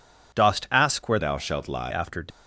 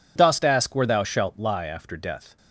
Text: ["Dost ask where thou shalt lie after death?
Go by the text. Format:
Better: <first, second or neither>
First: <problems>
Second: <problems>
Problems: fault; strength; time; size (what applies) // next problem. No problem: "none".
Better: second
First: changes voice from "thou" to "lie"; from 1.1 to 1.8 s; 0.7 s long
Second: none